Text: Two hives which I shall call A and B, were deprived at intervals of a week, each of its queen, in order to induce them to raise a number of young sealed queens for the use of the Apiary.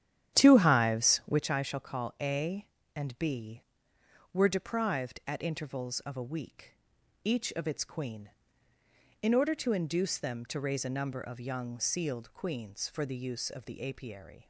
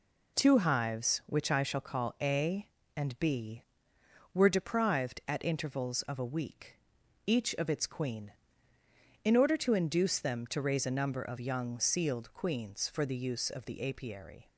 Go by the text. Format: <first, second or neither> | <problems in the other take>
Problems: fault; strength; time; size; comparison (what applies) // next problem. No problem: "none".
second | starts louder than the rest; strong; until 1.4 s; 10.5 dB